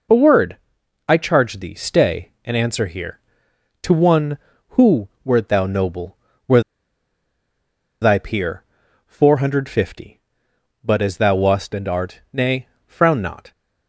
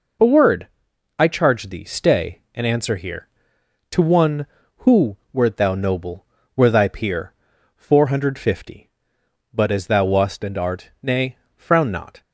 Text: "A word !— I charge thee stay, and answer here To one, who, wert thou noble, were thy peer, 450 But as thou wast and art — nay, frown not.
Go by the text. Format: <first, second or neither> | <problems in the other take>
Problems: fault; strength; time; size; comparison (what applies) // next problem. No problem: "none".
second | pauses between "were" and "thy"; strong; at 6.6 s; 1.4 s long